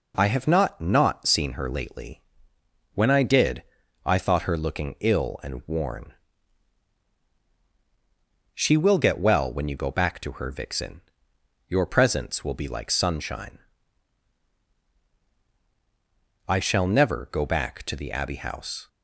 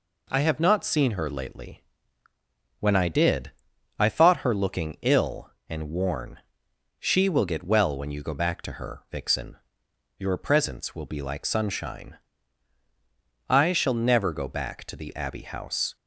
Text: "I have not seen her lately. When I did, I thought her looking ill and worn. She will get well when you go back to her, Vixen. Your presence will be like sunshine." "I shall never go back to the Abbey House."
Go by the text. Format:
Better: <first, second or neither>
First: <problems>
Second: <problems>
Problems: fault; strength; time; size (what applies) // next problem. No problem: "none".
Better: second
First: says "not" twice; at 0.7 s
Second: none